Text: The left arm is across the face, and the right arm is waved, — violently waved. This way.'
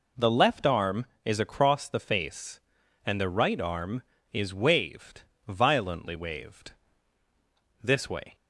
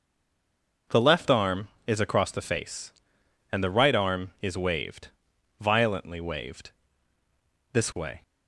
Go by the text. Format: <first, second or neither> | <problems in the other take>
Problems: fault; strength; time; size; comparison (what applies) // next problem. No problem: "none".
first | stays silent before the first word; slight; until 0.8 s; 0.8 s long